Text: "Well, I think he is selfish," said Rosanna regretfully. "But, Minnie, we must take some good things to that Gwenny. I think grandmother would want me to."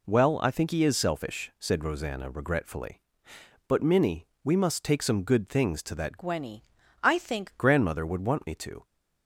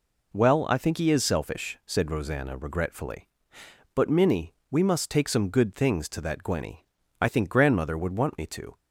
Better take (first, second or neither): second